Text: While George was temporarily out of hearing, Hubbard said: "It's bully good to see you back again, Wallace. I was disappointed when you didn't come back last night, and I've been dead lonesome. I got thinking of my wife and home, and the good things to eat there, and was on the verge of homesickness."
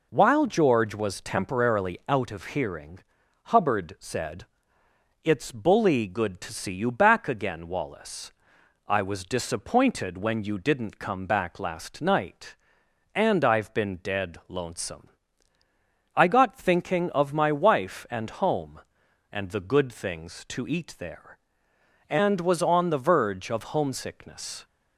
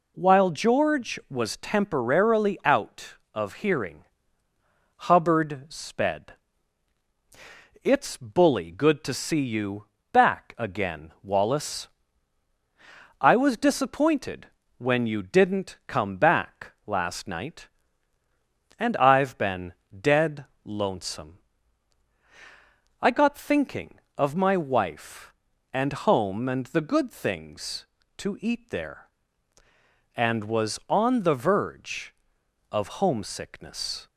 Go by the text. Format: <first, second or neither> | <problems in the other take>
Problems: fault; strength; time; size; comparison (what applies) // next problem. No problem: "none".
first | says "sped" for "said"; at 5.6 s // pauses between "you" and "back"; slight; at 9.8 s; 0.26 s long // pauses between "disappointed" and "when"; slight; at 14.4 s; 0.32 s long // pauses between "back" and "last"; slight; at 16.7 s; 0.16 s long // pauses between "been" and "dead"; slight; at 19.7 s; 0.18 s long // pauses between "dead" and "lonesome"; slight; at 20.4 s; 0.20 s long